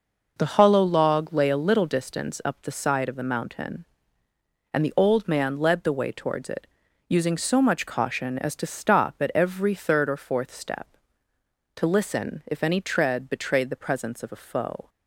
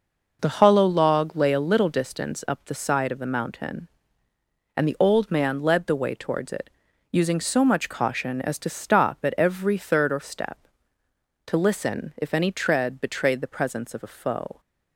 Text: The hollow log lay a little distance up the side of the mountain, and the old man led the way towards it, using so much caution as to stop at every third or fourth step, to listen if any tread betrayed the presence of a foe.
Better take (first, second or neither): first